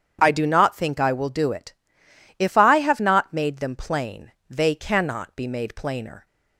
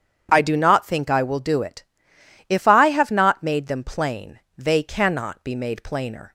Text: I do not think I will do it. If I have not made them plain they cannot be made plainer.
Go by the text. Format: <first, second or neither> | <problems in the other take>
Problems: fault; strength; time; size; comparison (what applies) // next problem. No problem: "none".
neither | starts louder than the rest; strong; the same in both // pauses between "plain" and "they"; slight; the same in both